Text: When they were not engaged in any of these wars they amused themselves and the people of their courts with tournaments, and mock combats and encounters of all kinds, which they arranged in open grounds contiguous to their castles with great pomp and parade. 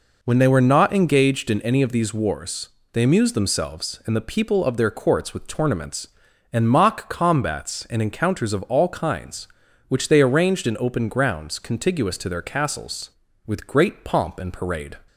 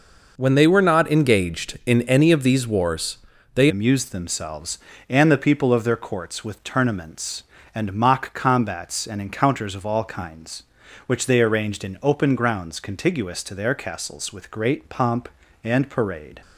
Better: first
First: pauses between "wars" and "they"; slight; at 2.6 s; 0.24 s long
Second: pauses between "wars" and "they"; slight; at 3.1 s; 0.36 s long // changes voice at "amused"; from 3.6 s on; 12.8 s long

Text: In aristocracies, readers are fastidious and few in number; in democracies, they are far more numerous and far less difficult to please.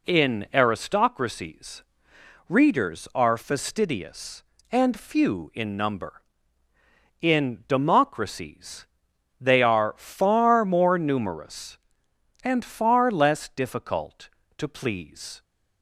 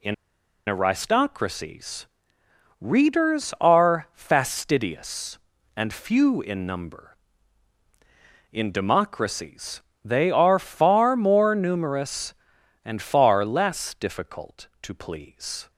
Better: first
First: none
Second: pauses between "In" and "aristocracies"; noticeable; at 0.1 s; 0.53 s long

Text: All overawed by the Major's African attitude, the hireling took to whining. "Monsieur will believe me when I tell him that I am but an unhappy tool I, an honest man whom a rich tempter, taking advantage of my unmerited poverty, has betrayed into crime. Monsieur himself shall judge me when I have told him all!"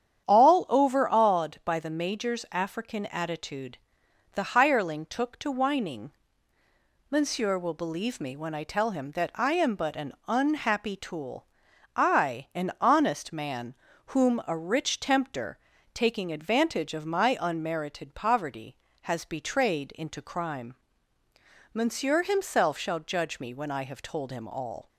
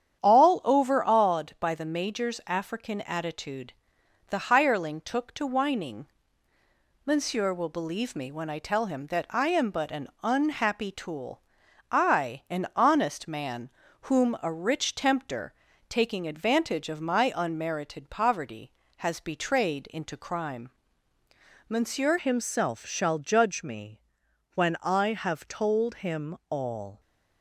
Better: first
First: starts louder than the rest; strong; until 1.3 s; 9 dB // pauses between "tool" and "I"; noticeable; at 11.4 s; 0.48 s long // pauses between "man" and "whom"; slight; at 13.7 s; 0.34 s long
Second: starts louder than the rest; strong; until 1.2 s; 9 dB // pauses between "tool" and "I"; noticeable; at 11.4 s; 0.48 s long // pauses between "man" and "whom"; slight; at 13.6 s; 0.34 s long // changes voice at "himself"; from 22.1 s on; 4.8 s long // pauses between "me" and "when"; noticeable; at 24.0 s; 0.52 s long

